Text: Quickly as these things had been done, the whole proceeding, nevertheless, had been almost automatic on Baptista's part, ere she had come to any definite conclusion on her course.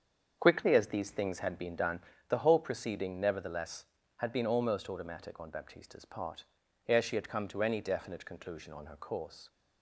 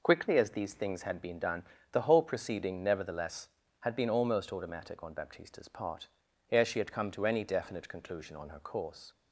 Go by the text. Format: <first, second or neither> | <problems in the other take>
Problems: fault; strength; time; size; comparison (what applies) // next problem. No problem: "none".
second | starts louder than the rest; strong; until 2.2 s; 7 dB